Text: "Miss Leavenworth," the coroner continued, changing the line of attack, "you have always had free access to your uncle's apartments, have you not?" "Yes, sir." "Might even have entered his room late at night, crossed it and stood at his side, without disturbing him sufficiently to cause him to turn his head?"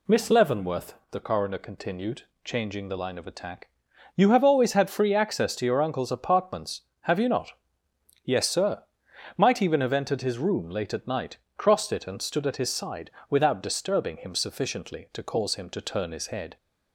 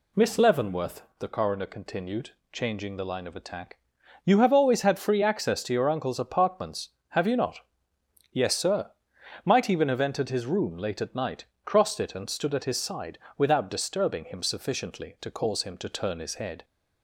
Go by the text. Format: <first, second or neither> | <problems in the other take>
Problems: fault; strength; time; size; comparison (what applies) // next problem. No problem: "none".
neither | none